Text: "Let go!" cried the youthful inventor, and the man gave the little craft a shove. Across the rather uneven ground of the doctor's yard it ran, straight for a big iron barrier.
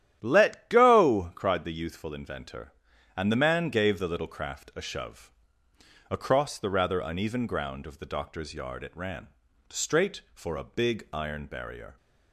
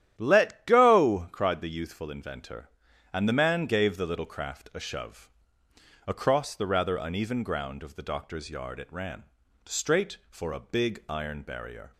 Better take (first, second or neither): neither